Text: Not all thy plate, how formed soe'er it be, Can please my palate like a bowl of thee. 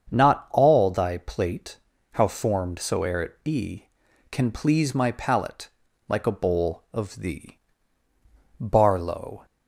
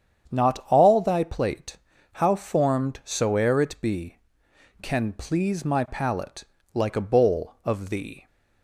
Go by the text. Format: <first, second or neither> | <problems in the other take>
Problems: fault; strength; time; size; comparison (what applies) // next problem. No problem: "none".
second | starts louder than the rest; strong; until 1.1 s; 7 dB; strong in the second // pauses between "palate" and "like"; at 5.6 s; 0.40 s long; slight in the second // goes on to say "BARLOW"; noticeable; from 8.5 s on; 0.88 s long